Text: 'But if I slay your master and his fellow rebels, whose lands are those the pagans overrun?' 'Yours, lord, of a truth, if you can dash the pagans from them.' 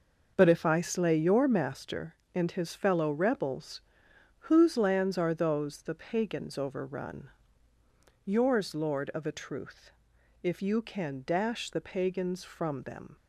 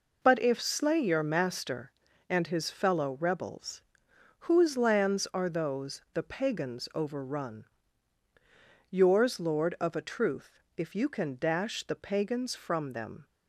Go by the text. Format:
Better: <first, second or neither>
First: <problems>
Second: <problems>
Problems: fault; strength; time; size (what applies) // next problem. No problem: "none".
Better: first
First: none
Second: skips "I"; at 0.6 s